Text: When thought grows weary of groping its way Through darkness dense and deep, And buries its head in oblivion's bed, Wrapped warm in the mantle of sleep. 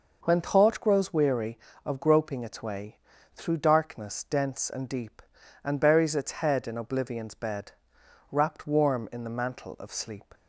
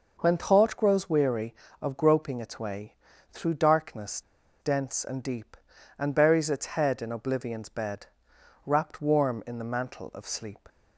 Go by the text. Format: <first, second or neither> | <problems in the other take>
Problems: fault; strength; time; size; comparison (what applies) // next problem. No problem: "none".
first | pauses between "way" and "Through"; slight; at 2.9 s; 0.36 s long; slight in the first // pauses between "darkness" and "dense"; at 4.2 s; 0.39 s long